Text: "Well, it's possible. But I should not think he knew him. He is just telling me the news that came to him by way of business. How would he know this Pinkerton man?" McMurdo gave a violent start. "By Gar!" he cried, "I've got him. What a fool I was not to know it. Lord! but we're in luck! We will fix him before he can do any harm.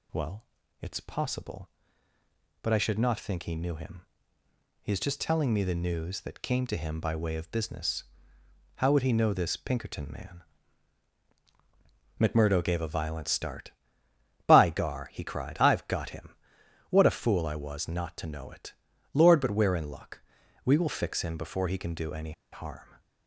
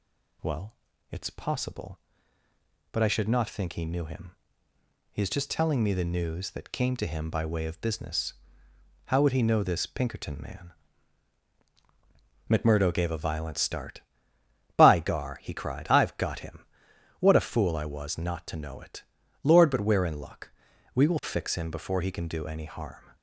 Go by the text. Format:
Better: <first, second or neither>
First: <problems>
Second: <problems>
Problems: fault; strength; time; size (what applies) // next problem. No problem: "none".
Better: second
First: pauses between "any" and "harm"; slight; at 22.3 s; 0.20 s long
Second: none